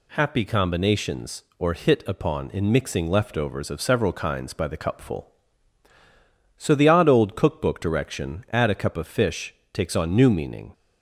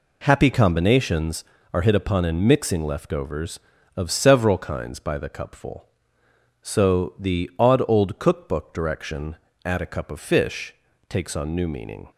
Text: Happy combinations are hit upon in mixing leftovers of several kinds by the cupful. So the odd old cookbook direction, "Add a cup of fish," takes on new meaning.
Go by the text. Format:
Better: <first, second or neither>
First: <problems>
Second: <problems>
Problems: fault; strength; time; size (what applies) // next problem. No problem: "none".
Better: second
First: says "or" for "are"; at 1.6 s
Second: none